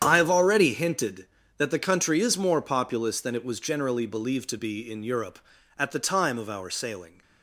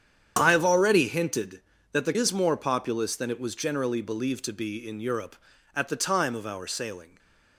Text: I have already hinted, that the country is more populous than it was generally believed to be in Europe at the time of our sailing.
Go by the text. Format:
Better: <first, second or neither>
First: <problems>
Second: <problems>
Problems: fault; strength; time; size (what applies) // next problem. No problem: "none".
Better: first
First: starts louder than the rest; strong; until 1.0 s; 9 dB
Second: starts louder than the rest; strong; until 1.4 s; 8.5 dB // skips "country"; at 2.1 s // stays silent after the last word; slight; from 7.0 s on; 0.5 s long